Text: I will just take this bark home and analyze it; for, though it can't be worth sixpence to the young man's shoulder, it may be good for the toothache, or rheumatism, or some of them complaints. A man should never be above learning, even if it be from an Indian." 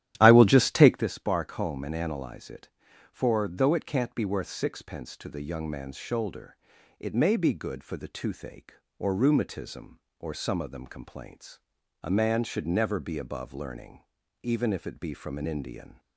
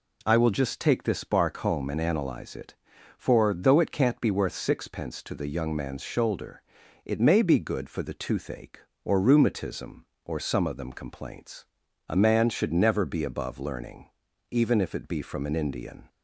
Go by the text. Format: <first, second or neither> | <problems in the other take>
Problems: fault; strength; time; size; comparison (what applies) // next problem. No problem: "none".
second | starts louder than the rest; strong; until 1.0 s; 12 dB